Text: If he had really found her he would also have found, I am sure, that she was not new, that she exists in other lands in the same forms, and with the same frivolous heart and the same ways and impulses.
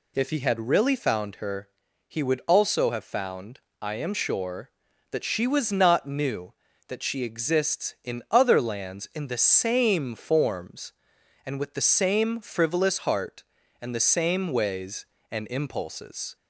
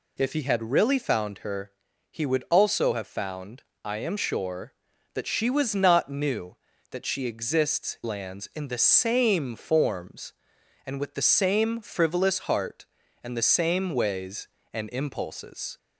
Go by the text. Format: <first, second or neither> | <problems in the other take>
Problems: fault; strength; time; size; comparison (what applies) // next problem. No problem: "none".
first | pauses between "her" and "he"; at 1.6 s; 0.40 s long; also in the first // skips "in other"; at 8.0 s